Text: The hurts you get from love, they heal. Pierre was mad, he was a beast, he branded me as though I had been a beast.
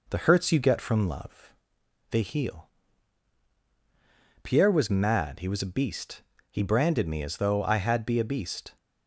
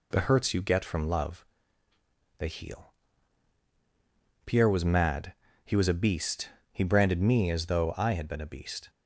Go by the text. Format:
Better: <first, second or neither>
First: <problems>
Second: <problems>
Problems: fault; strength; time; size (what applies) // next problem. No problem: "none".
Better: second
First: says "be" for "been"; at 8.0 s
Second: none